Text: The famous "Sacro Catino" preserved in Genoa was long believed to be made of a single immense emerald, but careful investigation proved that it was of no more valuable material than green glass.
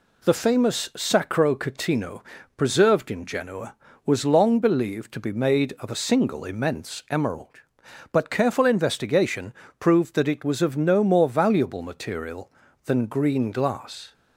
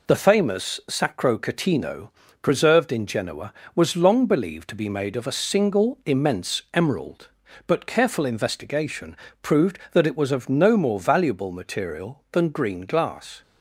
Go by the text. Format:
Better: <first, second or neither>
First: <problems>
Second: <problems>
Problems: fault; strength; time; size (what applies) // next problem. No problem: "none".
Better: first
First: pauses between "Catino" and "preserved"; slight; at 2.2 s; 0.34 s long // pauses between "investigation" and "proved"; slight; at 9.5 s; 0.28 s long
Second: gets quieter; noticeable; throughout; 5 dB // pauses between "Catino" and "preserved"; slight; at 2.0 s; 0.34 s long // pauses between "investigation" and "proved"; slight; at 9.1 s; 0.26 s long